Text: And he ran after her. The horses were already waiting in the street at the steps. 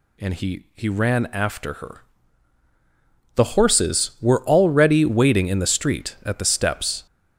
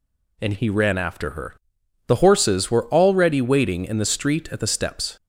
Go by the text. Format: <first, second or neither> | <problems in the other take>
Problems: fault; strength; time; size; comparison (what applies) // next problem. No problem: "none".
second | says "he" twice; at 0.7 s